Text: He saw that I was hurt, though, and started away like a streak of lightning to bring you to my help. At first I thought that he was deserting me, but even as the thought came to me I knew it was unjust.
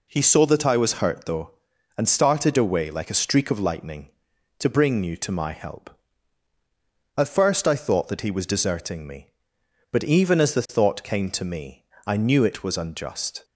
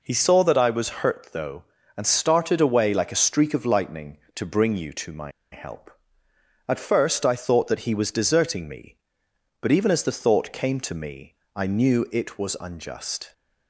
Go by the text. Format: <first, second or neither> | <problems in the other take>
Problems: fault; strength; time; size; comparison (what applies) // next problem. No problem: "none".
first | pauses between "my" and "help"; slight; at 5.3 s; 0.21 s long // pauses between "me" and "I"; slight; at 11.3 s; 0.20 s long; slight in the first